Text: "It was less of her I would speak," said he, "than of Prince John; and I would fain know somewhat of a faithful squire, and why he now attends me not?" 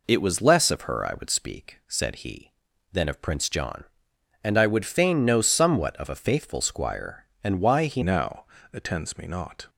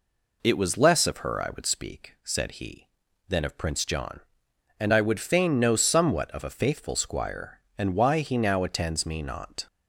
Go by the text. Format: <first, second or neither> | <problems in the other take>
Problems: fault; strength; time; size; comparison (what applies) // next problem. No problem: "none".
second | changes voice at "now"; from 8.0 s on; 1.6 s long // pauses between "now" and "attends"; slight; at 8.4 s; 0.26 s long